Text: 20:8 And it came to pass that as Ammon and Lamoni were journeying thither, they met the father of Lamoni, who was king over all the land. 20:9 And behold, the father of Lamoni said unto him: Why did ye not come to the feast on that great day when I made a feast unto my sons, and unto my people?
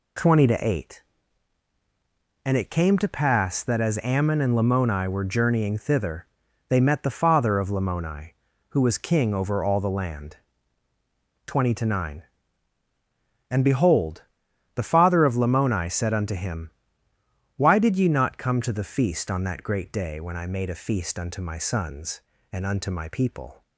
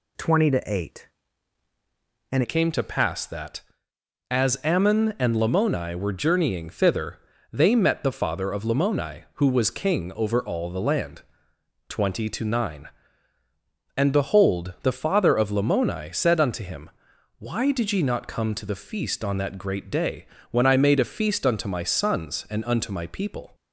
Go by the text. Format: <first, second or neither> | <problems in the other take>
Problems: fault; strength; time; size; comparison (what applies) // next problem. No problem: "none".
first | changes voice at "it"; from 2.4 s on; 21.1 s long // pauses between "day" and "when"; slight; at 20.2 s; 0.26 s long